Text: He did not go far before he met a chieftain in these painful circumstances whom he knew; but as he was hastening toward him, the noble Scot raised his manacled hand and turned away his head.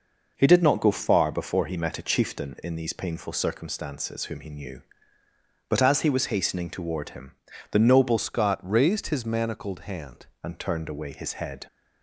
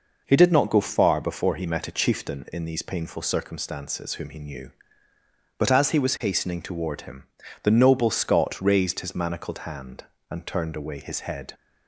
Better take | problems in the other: second | changes voice from "Scot" to "hand"; from 8.1 to 10.2 s; 2.1 s long

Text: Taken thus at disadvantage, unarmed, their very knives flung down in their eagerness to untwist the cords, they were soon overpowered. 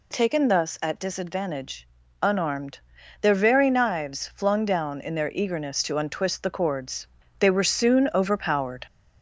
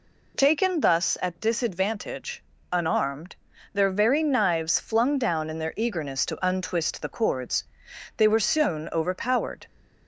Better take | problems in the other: second | gets louder; slight; throughout; 2.5 dB

